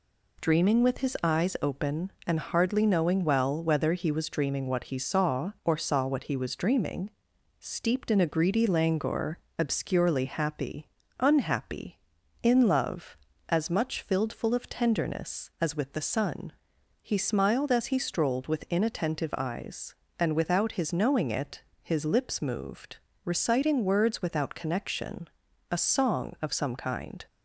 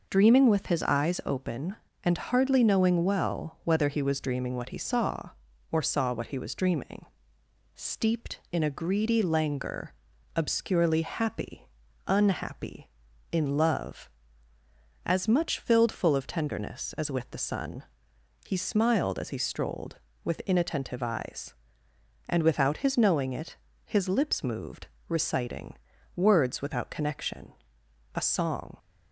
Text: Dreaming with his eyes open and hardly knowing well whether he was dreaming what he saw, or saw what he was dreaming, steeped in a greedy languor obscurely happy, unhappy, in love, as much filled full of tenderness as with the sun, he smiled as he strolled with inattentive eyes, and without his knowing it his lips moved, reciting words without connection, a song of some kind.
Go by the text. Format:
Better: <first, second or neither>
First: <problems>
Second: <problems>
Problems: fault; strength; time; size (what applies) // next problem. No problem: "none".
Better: first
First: pauses between "languor" and "obscurely"; slight; at 9.3 s; 0.18 s long // pauses between "it" and "his"; slight; at 21.6 s; 0.20 s long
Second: pauses between "languor" and "obscurely"; at 9.9 s; 0.44 s long // pauses between "it" and "his"; slight; at 23.5 s; 0.28 s long // pauses between "reciting" and "words"; at 25.7 s; 0.38 s long // stops before "of some kind"; at 28.7 s